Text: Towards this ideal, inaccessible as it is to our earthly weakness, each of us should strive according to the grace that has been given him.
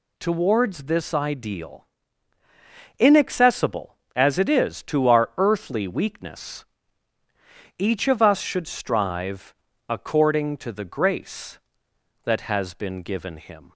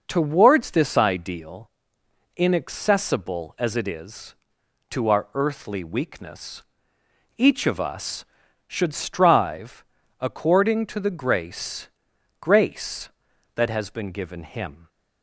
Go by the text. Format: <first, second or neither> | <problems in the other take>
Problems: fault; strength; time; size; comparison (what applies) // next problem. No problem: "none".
first | pauses between "strive" and "according"; slight; at 9.8 s; 0.36 s long; slight in the first // says "grace" twice; at 12.4 s